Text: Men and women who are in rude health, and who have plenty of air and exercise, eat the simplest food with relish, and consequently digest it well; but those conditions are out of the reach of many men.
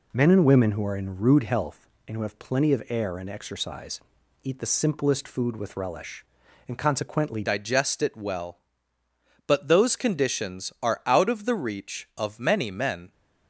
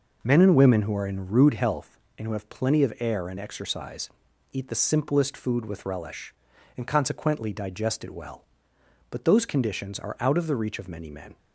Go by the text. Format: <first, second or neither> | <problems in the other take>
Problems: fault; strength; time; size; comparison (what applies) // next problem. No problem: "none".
second | changes voice at "digest"; from 7.4 s on; 5.7 s long